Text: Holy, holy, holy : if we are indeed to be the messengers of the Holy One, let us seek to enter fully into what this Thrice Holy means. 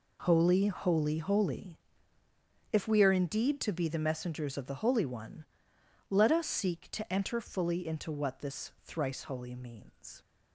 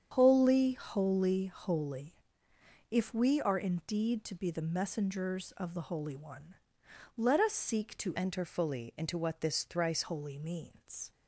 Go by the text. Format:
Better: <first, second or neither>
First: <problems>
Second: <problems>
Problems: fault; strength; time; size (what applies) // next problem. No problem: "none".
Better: first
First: none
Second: starts louder than the rest; strong; until 1.1 s; 8 dB // changes voice from "enter" to "Thrice"; from 8.1 to 10.0 s; 1.9 s long